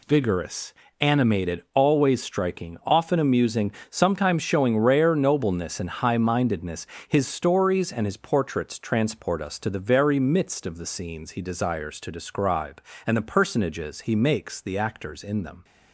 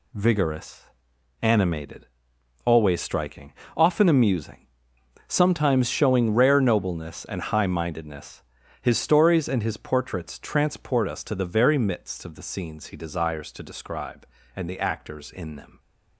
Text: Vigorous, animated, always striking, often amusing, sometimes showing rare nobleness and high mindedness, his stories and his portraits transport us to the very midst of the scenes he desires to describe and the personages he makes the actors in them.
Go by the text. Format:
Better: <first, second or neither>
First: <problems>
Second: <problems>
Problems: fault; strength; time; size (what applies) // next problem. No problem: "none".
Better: first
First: none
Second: skips "the personages he makes"; at 14.6 s